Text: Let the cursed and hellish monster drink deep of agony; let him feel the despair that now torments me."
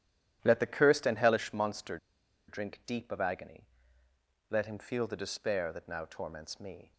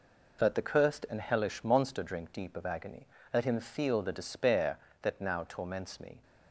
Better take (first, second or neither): second